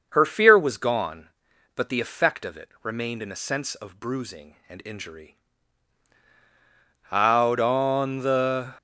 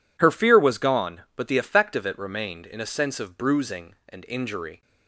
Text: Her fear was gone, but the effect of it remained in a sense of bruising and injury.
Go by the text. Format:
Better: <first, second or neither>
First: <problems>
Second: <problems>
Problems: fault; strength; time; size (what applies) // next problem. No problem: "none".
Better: second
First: starts louder than the rest; until 1.1 s; 6.5 dB // goes on to say "Out on the"; from 7.1 s on; 1.6 s long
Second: none